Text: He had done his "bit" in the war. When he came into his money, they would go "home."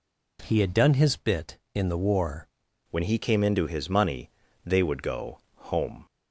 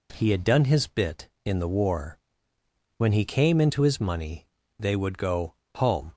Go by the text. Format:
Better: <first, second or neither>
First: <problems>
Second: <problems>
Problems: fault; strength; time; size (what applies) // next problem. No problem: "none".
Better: second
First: changes voice at "When"; from 2.9 s on; 3.1 s long // pauses between "go" and "home"; slight; at 5.3 s; 0.16 s long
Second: pauses between "go" and "home"; slight; at 5.5 s; 0.22 s long